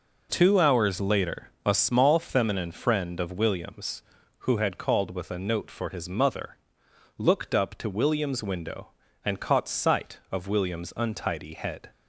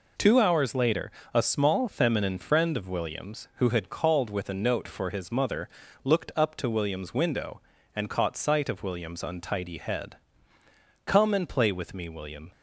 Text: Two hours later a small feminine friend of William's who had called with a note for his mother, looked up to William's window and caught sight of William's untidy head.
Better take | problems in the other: first | pauses between "later" and "a"; slight; at 1.1 s; 0.20 s long; slight in the first // goes on to say "Come and play with me William"; from 11.0 s on; 1.4 s long

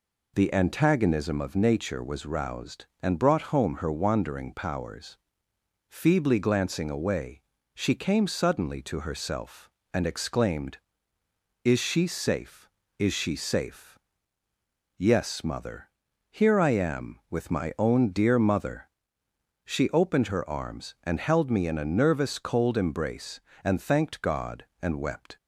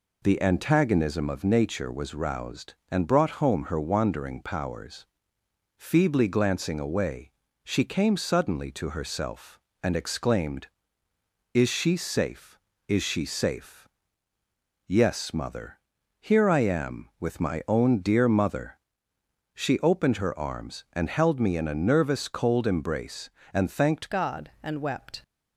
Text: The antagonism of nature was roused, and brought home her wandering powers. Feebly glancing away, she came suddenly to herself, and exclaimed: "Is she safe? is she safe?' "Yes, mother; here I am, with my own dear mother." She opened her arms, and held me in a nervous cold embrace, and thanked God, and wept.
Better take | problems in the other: first | changes voice at "God"; from 24.1 s on; 1.1 s long

